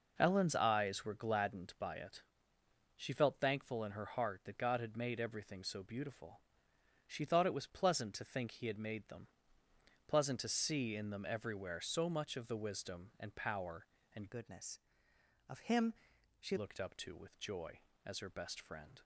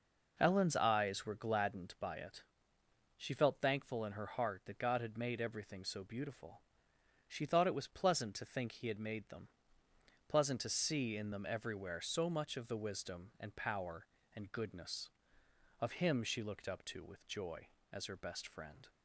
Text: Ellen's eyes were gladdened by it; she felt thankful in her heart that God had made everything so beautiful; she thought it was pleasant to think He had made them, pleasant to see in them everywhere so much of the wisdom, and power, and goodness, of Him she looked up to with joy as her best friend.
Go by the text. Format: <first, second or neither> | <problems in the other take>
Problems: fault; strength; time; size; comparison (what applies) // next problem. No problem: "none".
second | changes voice from "goodness" to "she"; from 14.3 to 16.5 s; 2.2 s long // pauses between "Him" and "she"; noticeable; at 15.9 s; 0.46 s long